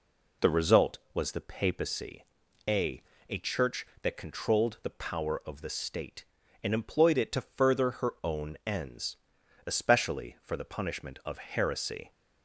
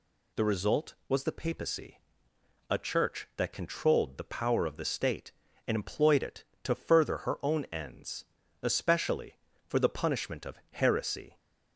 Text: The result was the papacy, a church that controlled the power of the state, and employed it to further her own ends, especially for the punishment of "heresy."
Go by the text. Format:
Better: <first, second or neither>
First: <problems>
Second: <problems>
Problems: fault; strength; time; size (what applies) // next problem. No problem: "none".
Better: second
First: says "a" twice; at 3.2 s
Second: none